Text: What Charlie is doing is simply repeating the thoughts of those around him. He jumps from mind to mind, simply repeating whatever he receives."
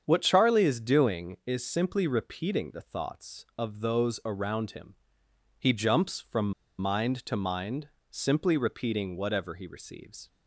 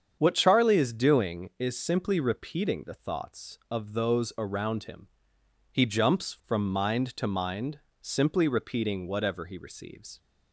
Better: second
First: starts louder than the rest; strong; until 1.0 s; 7.5 dB // pauses between "from" and "mind"; slight; at 6.5 s; 0.27 s long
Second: starts louder than the rest; strong; until 1.2 s; 7.5 dB

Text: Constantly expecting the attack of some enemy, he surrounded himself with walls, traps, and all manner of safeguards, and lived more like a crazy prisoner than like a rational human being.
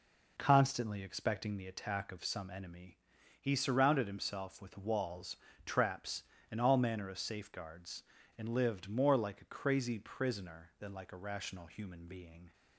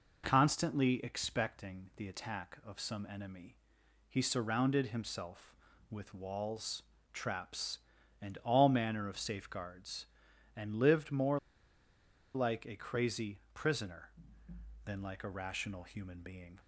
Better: first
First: none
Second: pauses between "more" and "like"; noticeable; at 11.3 s; 0.95 s long

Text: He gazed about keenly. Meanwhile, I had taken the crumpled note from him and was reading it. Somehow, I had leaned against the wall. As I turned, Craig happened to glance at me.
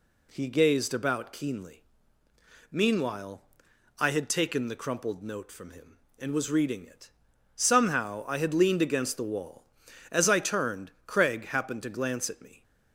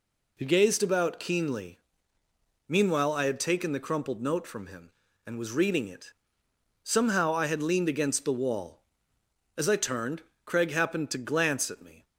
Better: neither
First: none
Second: none

